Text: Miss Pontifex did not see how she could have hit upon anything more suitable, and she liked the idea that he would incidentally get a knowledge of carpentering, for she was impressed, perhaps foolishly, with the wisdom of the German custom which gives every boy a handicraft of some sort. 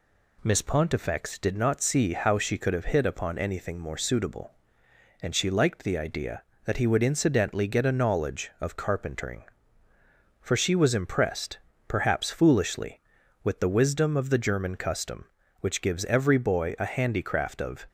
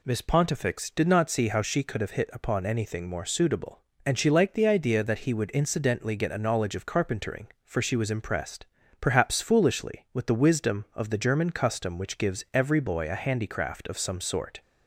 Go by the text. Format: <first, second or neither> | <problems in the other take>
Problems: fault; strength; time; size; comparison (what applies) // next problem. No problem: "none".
second | stops before "some sort"; at 17.8 s